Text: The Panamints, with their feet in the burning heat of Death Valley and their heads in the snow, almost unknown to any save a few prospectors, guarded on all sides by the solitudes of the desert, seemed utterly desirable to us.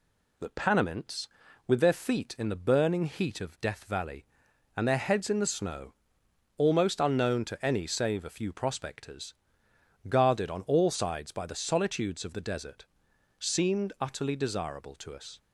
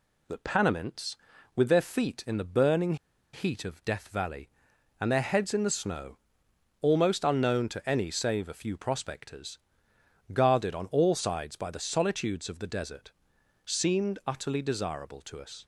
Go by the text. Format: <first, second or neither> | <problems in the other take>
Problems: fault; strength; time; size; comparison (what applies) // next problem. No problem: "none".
first | pauses between "burning" and "heat"; at 2.9 s; 0.38 s long